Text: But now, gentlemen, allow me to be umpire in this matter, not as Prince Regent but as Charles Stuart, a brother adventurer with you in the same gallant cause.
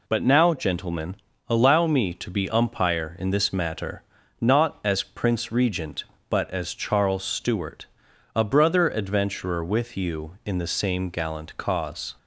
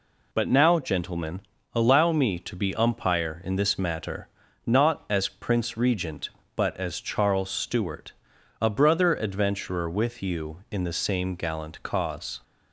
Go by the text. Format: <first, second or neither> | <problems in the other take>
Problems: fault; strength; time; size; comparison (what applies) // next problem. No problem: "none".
neither | none